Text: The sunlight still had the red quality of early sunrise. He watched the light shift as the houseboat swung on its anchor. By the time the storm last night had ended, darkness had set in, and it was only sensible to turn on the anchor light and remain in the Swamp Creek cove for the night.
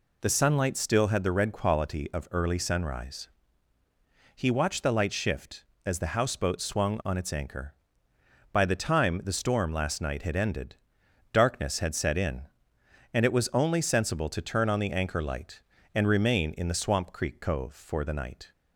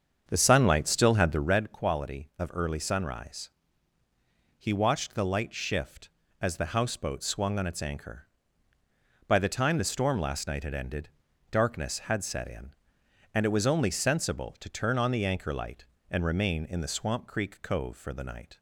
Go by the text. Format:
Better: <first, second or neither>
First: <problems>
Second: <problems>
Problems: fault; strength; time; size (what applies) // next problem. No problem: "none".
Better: first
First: none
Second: starts louder than the rest; strong; until 1.7 s; 7.5 dB